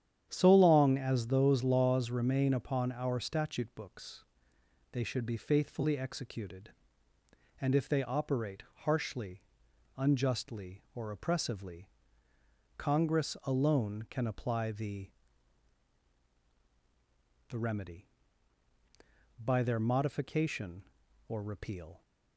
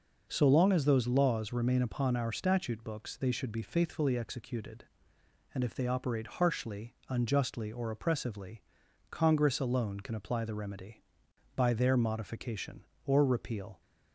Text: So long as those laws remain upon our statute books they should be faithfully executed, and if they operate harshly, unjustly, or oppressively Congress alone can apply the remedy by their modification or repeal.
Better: second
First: starts louder than the rest; strong; until 1.3 s; 9.5 dB // pauses between "books" and "they"; noticeable; at 4.2 s; 0.68 s long // pauses between "operate" and "harshly"; slight; at 8.6 s; 0.20 s long // pauses between "oppressively" and "Congress"; noticeable; at 11.8 s; 0.90 s long // says "the" twice; at 17.4 s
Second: pauses between "oppressively" and "Congress"; noticeable; at 8.6 s; 0.48 s long

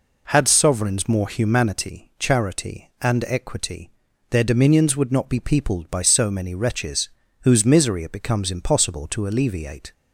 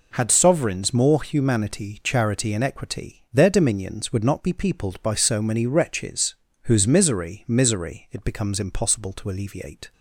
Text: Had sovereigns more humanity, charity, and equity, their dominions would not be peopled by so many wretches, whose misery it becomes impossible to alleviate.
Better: first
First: none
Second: says "misery" twice; at 7.4 s

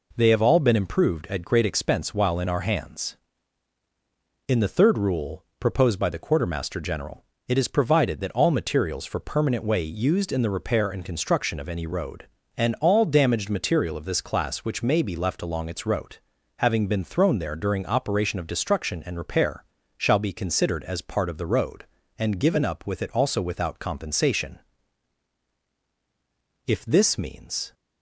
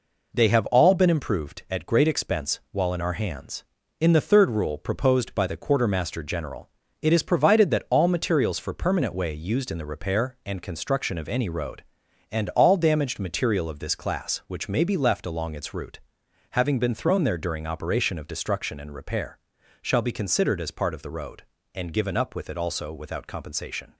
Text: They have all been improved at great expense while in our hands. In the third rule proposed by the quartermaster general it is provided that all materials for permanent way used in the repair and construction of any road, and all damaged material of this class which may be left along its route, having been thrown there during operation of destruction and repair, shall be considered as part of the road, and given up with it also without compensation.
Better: second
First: pauses between "rule" and "proposed"; slight; at 5.4 s; 0.16 s long // pauses between "general" and "it"; slight; at 7.2 s; 0.24 s long // goes on to say "If this means"; noticeable; from 26.6 s on; 1.0 s long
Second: pauses between "general" and "it"; slight; at 6.6 s; 0.32 s long

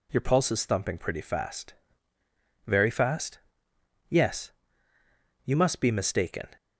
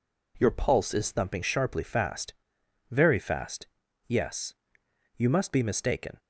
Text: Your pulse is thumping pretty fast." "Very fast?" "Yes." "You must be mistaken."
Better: first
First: none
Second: says "sharply" for "pretty"; at 1.4 s

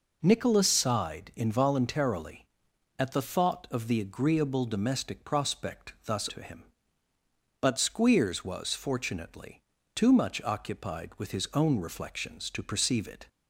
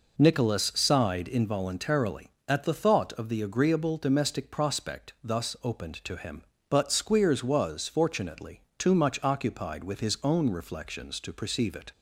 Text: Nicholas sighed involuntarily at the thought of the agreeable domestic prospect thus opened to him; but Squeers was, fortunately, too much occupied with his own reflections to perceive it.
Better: second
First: skips "opened"; at 6.2 s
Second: none

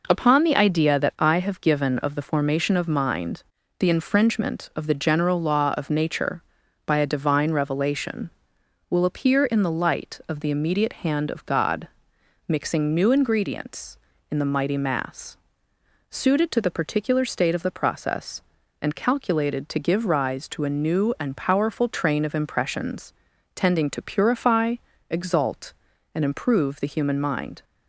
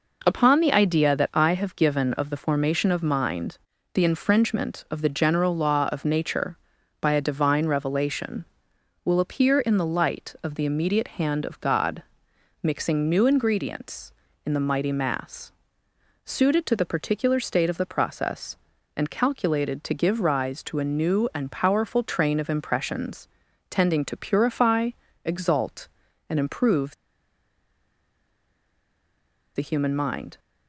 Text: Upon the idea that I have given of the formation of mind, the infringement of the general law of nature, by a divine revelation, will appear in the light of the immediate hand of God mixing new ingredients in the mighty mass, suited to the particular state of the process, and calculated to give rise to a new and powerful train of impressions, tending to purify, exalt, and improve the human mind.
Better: first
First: pauses between "God" and "mixing"; noticeable; at 11.8 s; 0.62 s long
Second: pauses between "God" and "mixing"; noticeable; at 12.0 s; 0.62 s long // pauses between "improve" and "the"; strong; at 26.9 s; 2.6 s long

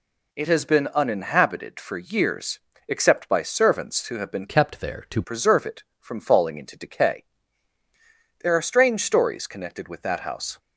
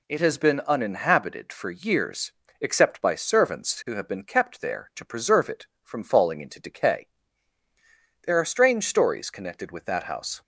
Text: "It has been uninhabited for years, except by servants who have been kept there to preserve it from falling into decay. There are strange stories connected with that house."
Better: second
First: changes voice from "kept" to "to"; from 4.4 to 5.2 s; 0.8 s long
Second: none

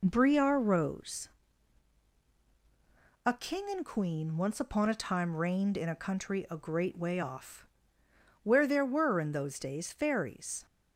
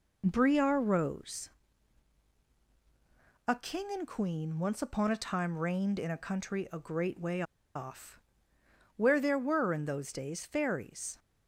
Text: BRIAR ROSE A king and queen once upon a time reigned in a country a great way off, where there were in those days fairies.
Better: first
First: pauses between "ROSE" and "A"; strong; at 1.2 s; 1.9 s long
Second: pauses between "ROSE" and "A"; strong; at 1.5 s; 1.9 s long // pauses between "way" and "off"; slight; at 7.4 s; 0.32 s long

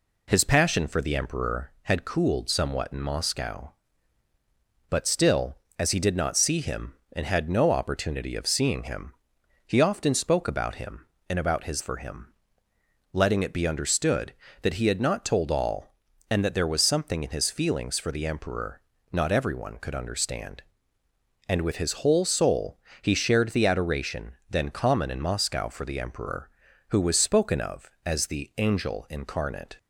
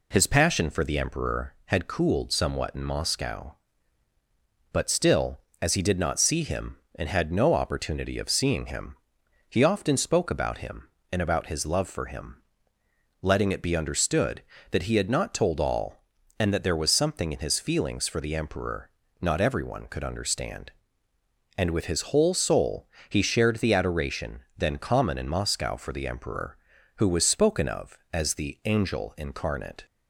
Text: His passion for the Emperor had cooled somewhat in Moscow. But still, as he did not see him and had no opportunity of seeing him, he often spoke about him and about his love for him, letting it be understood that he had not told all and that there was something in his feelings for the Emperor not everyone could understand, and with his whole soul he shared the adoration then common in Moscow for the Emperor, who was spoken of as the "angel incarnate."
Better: second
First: skips "love"; at 11.8 s // pauses between "Emperor" and "not"; slight; at 18.8 s; 0.32 s long // pauses between "soul" and "he"; slight; at 22.7 s; 0.24 s long // pauses between "adoration" and "then"; slight; at 24.3 s; 0.18 s long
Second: pauses between "Emperor" and "not"; slight; at 18.8 s; 0.32 s long // pauses between "soul" and "he"; slight; at 22.8 s; 0.22 s long // pauses between "adoration" and "then"; slight; at 24.4 s; 0.18 s long

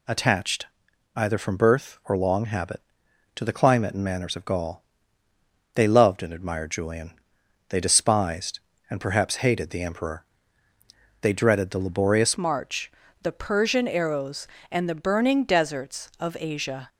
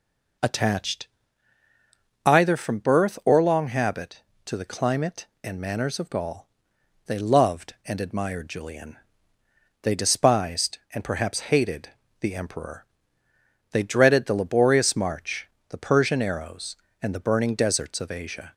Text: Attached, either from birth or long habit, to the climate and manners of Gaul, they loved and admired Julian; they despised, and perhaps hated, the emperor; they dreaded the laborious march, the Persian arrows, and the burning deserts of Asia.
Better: second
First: changes voice at "march"; from 12.3 s on; 4.5 s long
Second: none

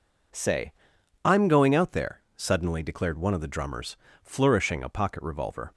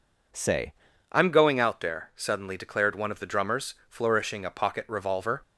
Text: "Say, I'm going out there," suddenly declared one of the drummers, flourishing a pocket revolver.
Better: first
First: none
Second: changes voice at "I'm"; from 1.1 s on; 4.3 s long

